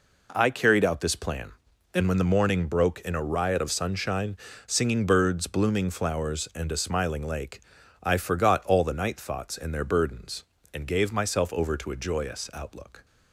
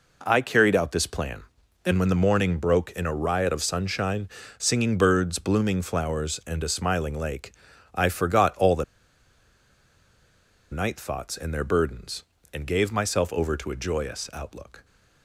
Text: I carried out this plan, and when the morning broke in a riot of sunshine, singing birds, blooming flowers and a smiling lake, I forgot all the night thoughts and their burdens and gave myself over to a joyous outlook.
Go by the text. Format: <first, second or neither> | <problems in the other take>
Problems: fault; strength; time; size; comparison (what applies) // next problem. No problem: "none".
first | pauses between "the" and "night"; strong; at 8.8 s; 1.8 s long